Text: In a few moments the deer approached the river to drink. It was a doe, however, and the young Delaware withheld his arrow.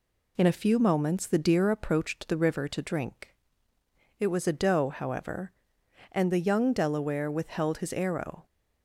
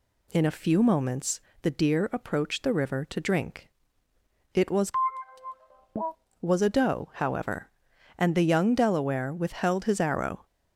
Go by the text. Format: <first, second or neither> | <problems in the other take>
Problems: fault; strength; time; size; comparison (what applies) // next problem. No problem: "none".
first | pauses between "moments" and "the"; slight; at 1.3 s; 0.22 s long // says "was" twice; at 6.4 s